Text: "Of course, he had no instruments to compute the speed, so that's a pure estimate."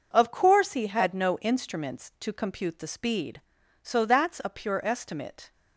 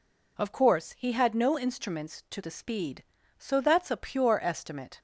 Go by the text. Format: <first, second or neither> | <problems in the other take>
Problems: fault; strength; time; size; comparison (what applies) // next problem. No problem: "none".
first | skips "compute"; at 2.4 s